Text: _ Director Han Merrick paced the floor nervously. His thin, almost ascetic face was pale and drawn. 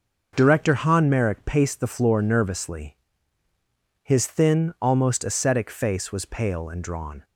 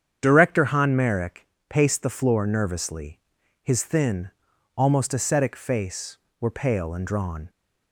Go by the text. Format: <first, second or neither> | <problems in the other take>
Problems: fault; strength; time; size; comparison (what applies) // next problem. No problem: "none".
first | starts louder than the rest; strong; until 1.2 s; 8 dB // pauses between "Merrick" and "paced"; slight; at 1.4 s; 0.22 s long // says "were" for "was"; at 6.3 s